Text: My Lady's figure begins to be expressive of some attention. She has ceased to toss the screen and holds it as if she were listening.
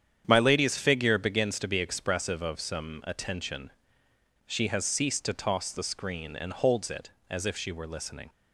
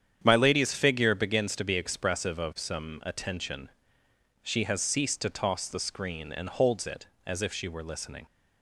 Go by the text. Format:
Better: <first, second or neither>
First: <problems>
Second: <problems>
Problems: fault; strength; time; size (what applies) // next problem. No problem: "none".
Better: neither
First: starts louder than the rest; strong; until 1.2 s; 9 dB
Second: starts louder than the rest; strong; until 1.2 s; 9 dB